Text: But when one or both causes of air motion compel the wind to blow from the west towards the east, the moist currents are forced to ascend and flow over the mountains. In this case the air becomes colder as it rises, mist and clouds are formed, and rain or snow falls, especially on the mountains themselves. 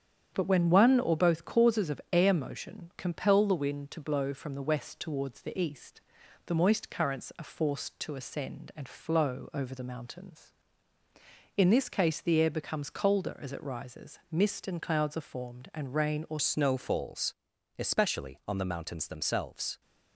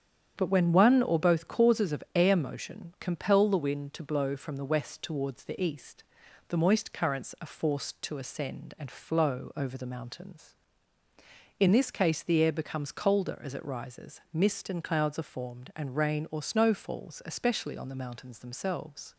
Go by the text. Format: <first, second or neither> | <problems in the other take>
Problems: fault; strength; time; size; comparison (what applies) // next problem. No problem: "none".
second | starts louder than the rest; strong; until 1.3 s; 8.5 dB; strong in the second // changes voice at "snow"; from 16.3 s on; 3.5 s long